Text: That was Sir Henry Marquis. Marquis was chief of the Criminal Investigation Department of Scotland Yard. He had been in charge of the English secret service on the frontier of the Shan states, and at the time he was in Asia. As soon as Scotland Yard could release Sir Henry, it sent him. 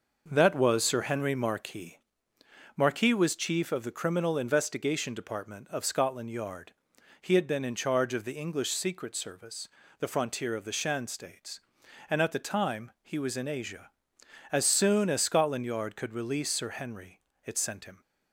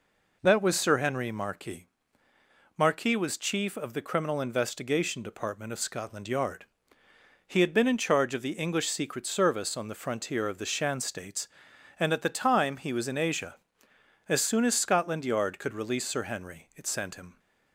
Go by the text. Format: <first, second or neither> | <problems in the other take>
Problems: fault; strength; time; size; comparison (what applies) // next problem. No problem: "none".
second | skips "on"; at 9.8 s